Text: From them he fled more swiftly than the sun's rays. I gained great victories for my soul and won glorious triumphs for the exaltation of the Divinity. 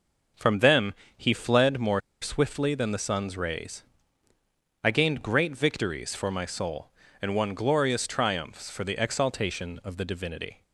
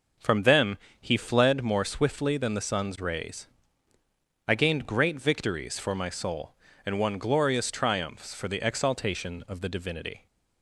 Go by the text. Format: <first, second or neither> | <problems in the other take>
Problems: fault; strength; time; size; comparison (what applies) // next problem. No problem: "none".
second | pauses between "them" and "he"; slight; at 0.9 s; 0.24 s long; slight in the second // pauses between "more" and "swiftly"; slight; at 2.0 s; 0.21 s long